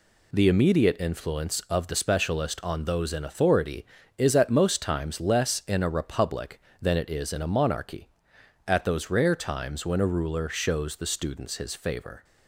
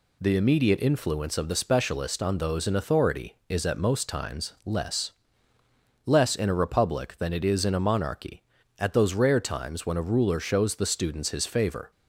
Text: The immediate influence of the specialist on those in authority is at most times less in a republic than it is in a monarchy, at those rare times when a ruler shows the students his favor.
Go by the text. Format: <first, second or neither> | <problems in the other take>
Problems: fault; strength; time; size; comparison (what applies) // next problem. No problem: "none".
first | says "less" twice; at 6.0 s